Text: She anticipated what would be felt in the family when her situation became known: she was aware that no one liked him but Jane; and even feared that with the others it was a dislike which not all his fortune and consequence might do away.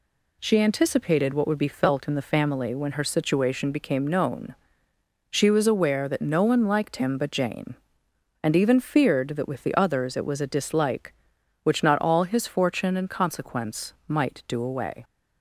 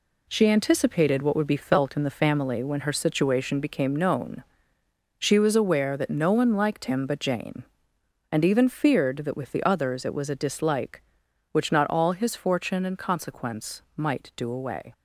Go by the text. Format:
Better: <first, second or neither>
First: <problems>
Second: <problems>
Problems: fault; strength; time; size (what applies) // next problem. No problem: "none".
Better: first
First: pauses between "consequence" and "might"; slight; at 13.9 s; 0.16 s long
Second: gets quieter; throughout; 6.5 dB // pauses between "consequence" and "might"; slight; at 13.8 s; 0.16 s long